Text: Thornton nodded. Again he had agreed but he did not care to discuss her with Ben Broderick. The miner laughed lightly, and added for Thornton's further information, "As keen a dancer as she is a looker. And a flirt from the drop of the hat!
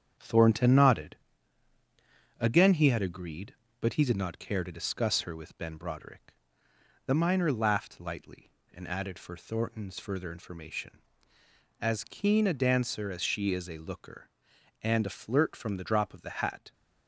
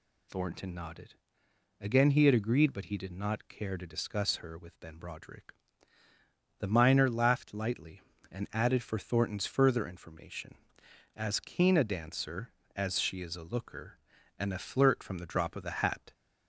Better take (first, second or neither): second